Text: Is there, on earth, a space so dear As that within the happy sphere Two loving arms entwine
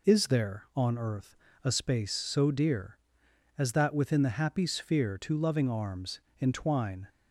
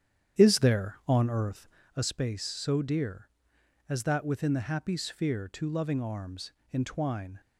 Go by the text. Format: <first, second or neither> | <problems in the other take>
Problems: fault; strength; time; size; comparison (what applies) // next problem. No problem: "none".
first | starts louder than the rest; strong; until 1.9 s; 9.5 dB // pauses between "arms" and "entwine"; slight; at 6.5 s; 0.20 s long; slight in the first